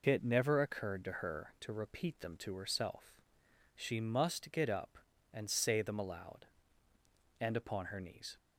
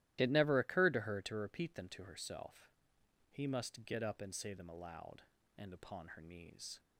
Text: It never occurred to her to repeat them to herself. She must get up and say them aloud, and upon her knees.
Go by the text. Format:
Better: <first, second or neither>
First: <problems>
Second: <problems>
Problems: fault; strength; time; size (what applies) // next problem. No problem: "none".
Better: first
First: none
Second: starts louder than the rest; strong; until 1.2 s; 14 dB // says "He" for "She"; at 3.3 s